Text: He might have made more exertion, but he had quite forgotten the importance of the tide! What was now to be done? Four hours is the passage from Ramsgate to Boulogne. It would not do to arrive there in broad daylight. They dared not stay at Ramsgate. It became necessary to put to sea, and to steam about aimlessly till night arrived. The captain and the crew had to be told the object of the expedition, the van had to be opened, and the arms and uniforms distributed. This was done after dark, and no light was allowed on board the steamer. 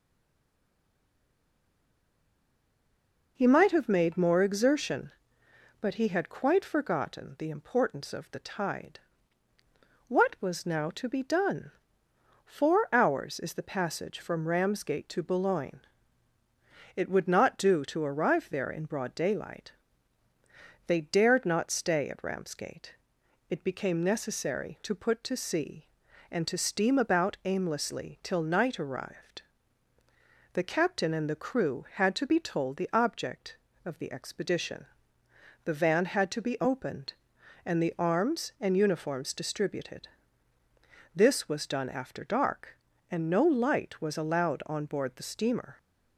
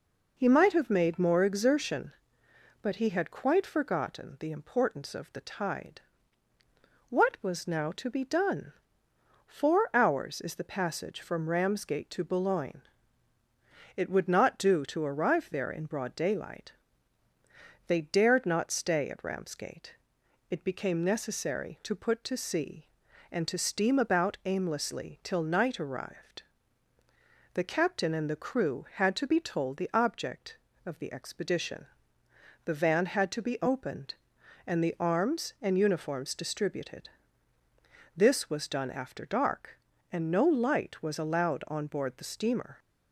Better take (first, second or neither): second